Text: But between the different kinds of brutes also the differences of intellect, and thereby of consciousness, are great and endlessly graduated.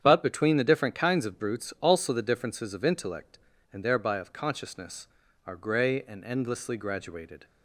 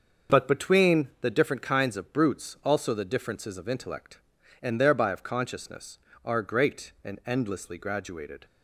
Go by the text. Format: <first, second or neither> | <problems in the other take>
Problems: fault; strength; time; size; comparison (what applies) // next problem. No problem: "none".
second | starts louder than the rest; strong; until 1.0 s; 8.5 dB; also in the second // says "grey" for "great"; at 5.5 s